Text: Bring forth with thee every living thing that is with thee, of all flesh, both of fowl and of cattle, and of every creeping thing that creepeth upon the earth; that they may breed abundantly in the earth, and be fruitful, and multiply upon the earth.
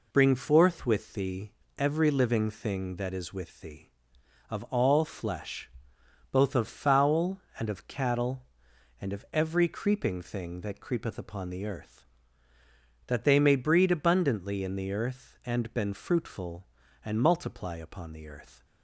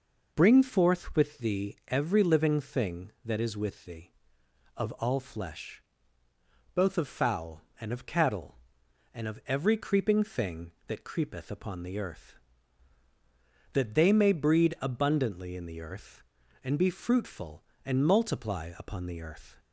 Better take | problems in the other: second | pauses between "thee" and "every"; slight; at 1.5 s; 0.26 s long // says "been" for "be"; at 15.7 s

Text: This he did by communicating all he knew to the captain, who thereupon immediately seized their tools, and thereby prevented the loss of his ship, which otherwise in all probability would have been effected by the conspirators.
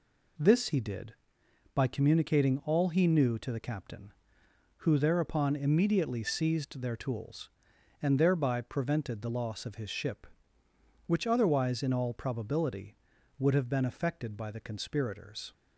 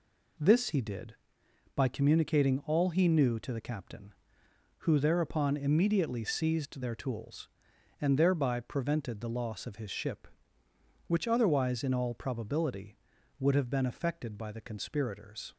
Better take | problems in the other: neither | none

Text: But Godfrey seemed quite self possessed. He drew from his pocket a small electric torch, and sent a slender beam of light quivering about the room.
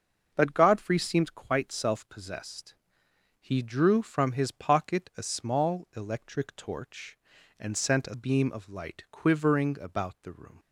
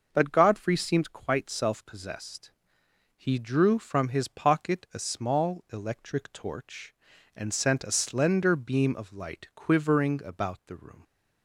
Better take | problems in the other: second | starts louder than the rest; until 1.3 s; 6.5 dB // skips "slender"; at 8.1 s

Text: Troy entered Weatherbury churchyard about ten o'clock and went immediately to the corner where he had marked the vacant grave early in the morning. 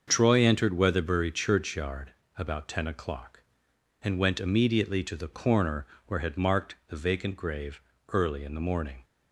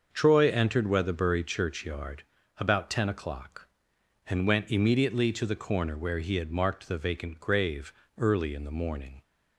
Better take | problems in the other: second | starts louder than the rest; until 1.0 s; 6.5 dB; also in the second // pauses between "churchyard" and "about"; slight; at 2.1 s; 0.22 s long; slight in the second // pauses between "corner" and "where"; slight; at 5.8 s; 0.22 s long // skips "he"; at 6.2 s // pauses between "grave" and "early"; slight; at 7.7 s; 0.30 s long; slight in the second

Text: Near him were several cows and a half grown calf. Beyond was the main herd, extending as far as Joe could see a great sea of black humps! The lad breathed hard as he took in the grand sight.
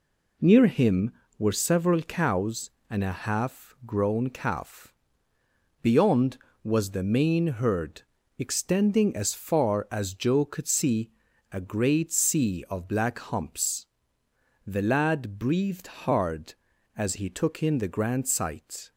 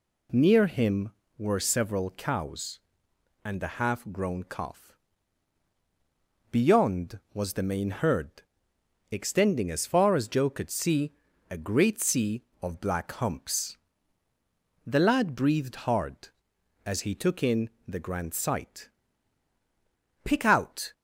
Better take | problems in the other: first | pauses between "see" and "a"; at 11.1 s; 0.38 s long; also in the first // pauses between "in" and "the"; slight; at 17.6 s; 0.20 s long // goes on to say "Pick out"; noticeable; from 20.2 s on; 0.70 s long

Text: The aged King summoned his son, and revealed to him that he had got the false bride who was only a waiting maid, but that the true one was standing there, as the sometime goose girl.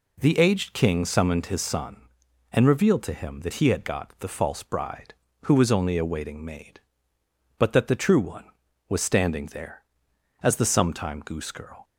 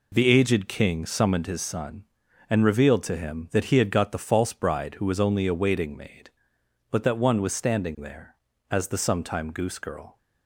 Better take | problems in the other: first | skips "the true"; at 7.1 s

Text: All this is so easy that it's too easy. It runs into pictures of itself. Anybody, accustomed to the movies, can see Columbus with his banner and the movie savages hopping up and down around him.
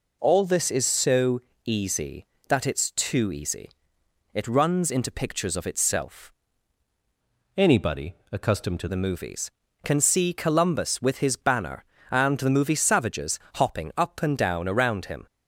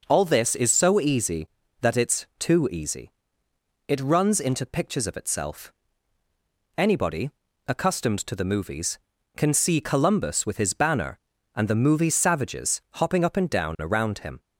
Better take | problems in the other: second | pauses between "so" and "easy"; slight; at 1.3 s; 0.24 s long // changes voice from "Anybody" to "to"; from 7.5 to 8.8 s; 1.3 s long // pauses between "savages" and "hopping"; slight; at 13.3 s; 0.18 s long

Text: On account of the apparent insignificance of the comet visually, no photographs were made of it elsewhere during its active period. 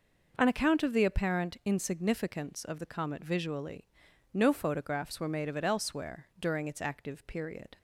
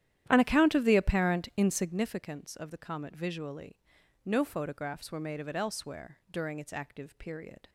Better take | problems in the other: first | starts louder than the rest; strong; until 2.1 s; 11.5 dB

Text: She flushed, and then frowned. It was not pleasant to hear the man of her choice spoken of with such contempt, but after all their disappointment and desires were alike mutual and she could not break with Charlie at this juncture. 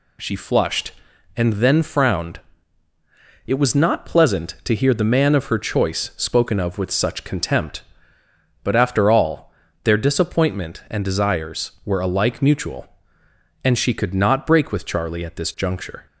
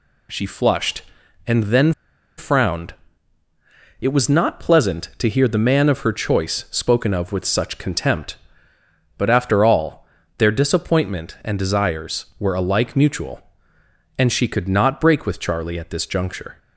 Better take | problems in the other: first | pauses between "then" and "frowned"; at 1.9 s; 0.45 s long // pauses between "all" and "their"; slight; at 10.0 s; 0.34 s long; slight in the first

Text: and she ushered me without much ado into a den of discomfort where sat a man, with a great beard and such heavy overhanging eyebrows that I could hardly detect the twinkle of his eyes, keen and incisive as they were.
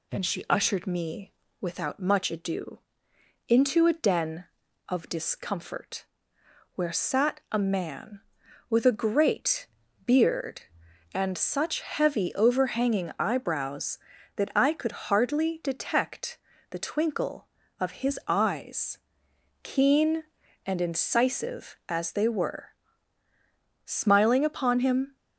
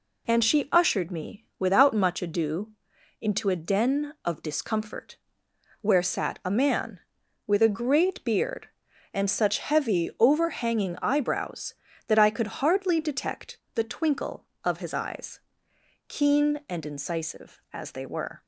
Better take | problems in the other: second | pauses between "me" and "without"; slight; at 1.3 s; 0.28 s long // pauses between "ado" and "into"; noticeable; at 2.7 s; 0.68 s long; noticeable in the second // pauses between "discomfort" and "where"; noticeable; at 6.0 s; 0.70 s long; noticeable in the second // pauses between "great" and "beard"; at 9.6 s; 0.40 s long // pauses between "detect" and "the"; slight; at 16.3 s; 0.32 s long; slight in the second // goes on to say "Smiling upon him"; noticeable; from 23.8 s on; 1.3 s long

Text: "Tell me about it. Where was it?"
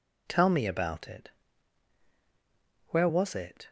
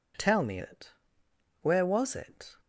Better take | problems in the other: first | skips "about"; at 0.5 s

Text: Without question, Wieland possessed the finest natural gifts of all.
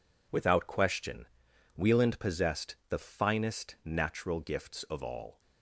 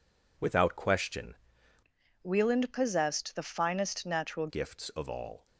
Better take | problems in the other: first | changes voice from "Wieland" to "natural"; from 2.2 to 4.4 s; 2.2 s long

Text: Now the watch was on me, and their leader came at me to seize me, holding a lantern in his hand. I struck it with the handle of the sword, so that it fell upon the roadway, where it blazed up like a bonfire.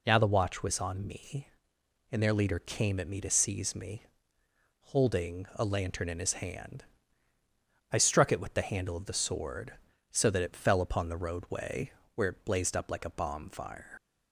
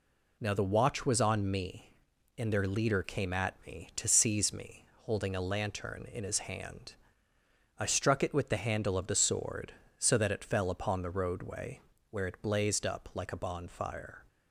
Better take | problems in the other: second | leaves "bonfire" unfinished; at 13.9 s; 65 ms

